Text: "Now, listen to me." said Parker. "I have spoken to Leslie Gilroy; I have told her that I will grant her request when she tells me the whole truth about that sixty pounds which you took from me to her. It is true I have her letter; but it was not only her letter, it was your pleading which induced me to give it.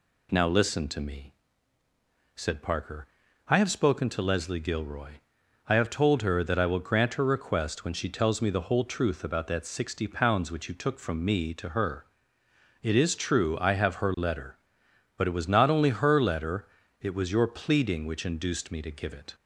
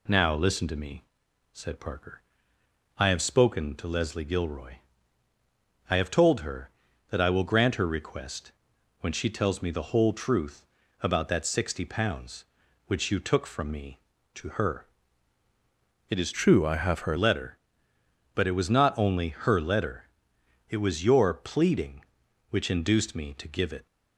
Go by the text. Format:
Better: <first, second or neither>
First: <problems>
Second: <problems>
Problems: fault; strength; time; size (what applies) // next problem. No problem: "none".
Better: first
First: none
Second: pauses between "request" and "when"; noticeable; at 8.5 s; 0.48 s long // pauses between "truth" and "about"; slight; at 10.6 s; 0.36 s long // changes voice from "true" to "her"; from 16.3 to 17.1 s; 0.8 s long